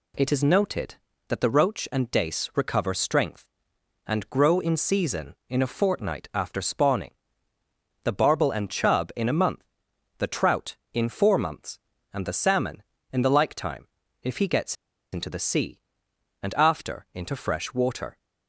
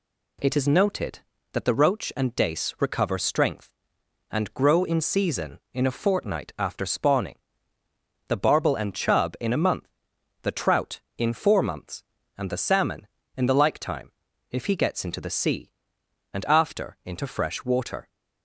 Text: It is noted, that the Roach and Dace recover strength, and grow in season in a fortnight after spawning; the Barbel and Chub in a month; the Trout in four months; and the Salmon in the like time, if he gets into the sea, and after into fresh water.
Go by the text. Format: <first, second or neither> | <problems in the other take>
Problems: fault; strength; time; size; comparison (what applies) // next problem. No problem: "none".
second | pauses between "gets" and "into"; at 14.7 s; 0.39 s long